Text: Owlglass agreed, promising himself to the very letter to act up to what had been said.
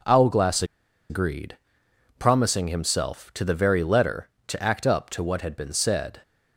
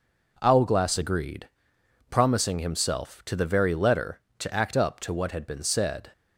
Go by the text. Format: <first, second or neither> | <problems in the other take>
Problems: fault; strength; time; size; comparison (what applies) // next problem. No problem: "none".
second | pauses between "Owlglass" and "agreed"; noticeable; at 0.6 s; 0.46 s long